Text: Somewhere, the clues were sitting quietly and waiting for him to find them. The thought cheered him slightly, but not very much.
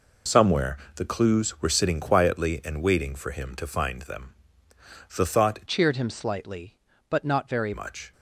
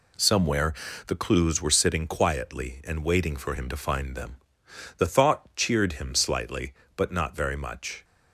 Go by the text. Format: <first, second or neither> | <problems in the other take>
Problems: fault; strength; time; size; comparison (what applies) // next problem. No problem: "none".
second | changes voice from "cheered" to "very"; from 5.6 to 7.7 s; 2.1 s long